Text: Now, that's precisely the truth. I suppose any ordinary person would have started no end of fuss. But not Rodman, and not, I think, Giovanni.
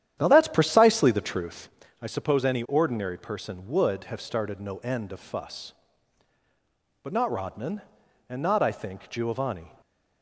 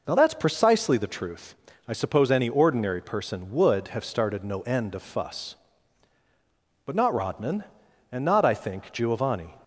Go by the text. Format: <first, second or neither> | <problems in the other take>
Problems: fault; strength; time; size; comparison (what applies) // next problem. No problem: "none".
second | starts louder than the rest; strong; until 1.9 s; 10.5 dB